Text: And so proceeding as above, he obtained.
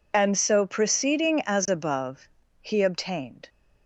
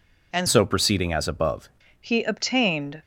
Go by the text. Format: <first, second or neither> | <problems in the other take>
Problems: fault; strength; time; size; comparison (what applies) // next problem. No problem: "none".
first | changes voice from "so" to "above"; from 0.4 to 1.6 s; 1.2 s long